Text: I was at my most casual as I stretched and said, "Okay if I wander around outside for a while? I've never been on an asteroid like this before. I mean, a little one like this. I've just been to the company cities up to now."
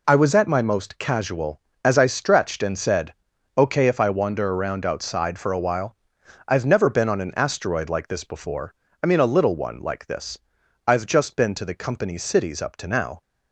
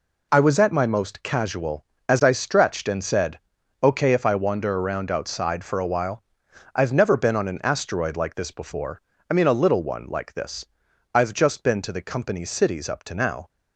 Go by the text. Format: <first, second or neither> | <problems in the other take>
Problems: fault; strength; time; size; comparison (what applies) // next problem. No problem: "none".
neither | none